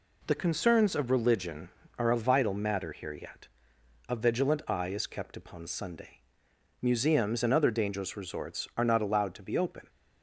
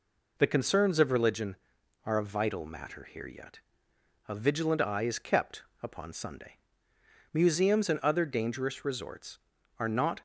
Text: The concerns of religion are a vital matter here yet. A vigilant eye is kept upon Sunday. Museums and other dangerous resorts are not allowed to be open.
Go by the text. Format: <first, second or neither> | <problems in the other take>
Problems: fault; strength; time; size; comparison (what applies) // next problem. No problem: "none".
first | pauses between "kept" and "upon"; slight; at 5.6 s; 0.18 s long // stops before "allowed to be open"; at 10.1 s